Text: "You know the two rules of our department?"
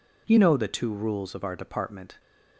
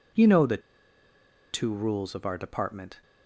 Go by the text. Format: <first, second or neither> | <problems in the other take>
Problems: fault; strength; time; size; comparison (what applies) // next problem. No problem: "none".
first | pauses between "the" and "two"; noticeable; at 0.5 s; 0.93 s long